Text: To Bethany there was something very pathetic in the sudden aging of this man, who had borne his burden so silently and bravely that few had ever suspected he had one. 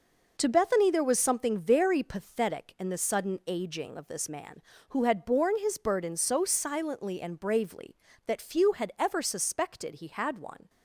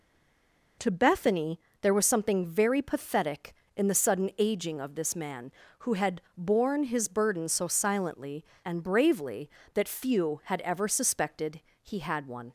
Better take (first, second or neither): first